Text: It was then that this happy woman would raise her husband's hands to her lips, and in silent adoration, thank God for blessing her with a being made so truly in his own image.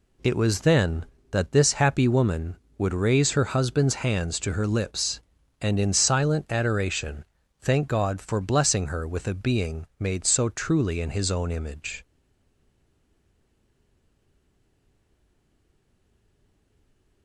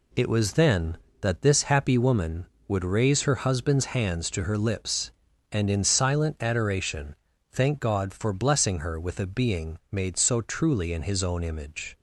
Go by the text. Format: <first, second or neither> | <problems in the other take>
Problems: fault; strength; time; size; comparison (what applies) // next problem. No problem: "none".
second | stays silent after the last word; strong; from 12.0 s on; 5.2 s long